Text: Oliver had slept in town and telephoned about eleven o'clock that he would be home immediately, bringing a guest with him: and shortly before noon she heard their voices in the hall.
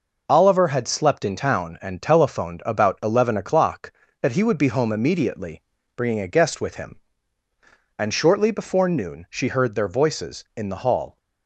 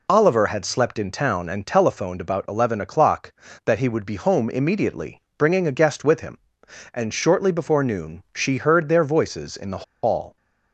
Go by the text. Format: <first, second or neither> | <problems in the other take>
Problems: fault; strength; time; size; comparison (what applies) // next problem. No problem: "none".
first | pauses between "the" and "hall"; slight; at 9.8 s; 0.21 s long